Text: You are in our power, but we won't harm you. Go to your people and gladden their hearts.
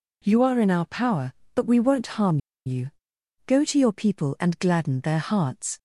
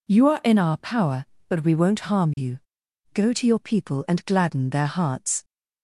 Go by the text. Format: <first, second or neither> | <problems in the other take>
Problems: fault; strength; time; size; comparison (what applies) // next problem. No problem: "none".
second | pauses between "harm" and "you"; slight; at 2.3 s; 0.28 s long